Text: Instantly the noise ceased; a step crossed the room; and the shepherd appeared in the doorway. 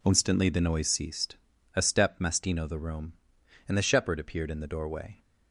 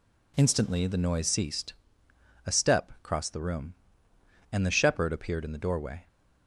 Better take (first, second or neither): second